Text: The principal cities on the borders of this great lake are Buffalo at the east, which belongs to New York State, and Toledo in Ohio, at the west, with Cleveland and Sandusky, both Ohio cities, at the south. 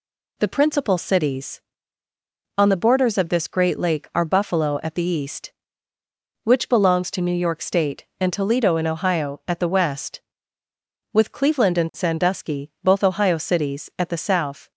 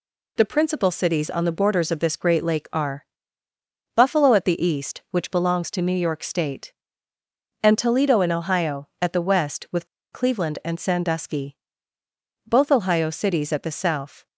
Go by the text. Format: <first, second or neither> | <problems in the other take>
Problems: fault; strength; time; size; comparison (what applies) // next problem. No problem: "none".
first | pauses between "are" and "Buffalo"; noticeable; at 3.0 s; 0.92 s long // pauses between "with" and "Cleveland"; slight; at 9.8 s; 0.25 s long